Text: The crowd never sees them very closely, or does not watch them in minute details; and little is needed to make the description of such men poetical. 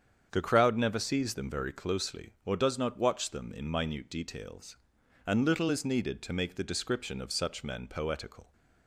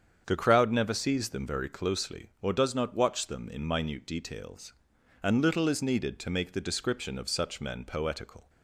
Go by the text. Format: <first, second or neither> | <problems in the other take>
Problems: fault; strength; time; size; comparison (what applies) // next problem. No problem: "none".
neither | starts louder than the rest; strong; the same in both